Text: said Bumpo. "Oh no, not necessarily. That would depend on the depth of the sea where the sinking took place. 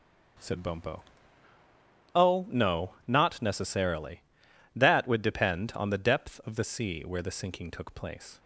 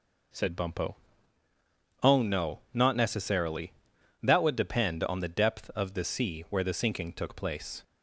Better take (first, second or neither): neither